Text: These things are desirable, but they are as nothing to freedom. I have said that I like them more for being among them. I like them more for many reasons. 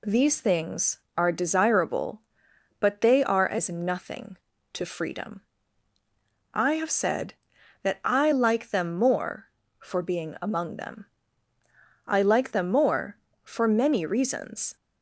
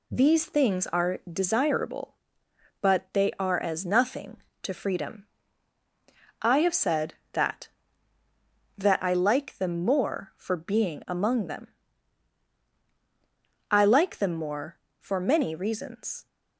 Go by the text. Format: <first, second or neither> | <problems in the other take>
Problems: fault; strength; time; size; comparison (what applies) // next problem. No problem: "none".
first | says "that" twice; at 8.7 s